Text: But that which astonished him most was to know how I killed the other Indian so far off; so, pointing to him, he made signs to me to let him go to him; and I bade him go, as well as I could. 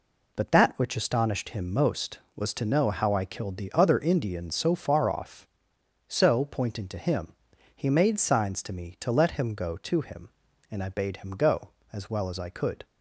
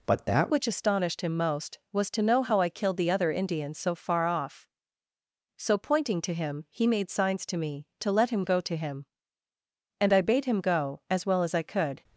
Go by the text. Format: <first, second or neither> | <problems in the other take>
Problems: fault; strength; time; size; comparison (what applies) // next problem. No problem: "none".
first | changes voice at "which"; from 0.5 s on; 11.5 s long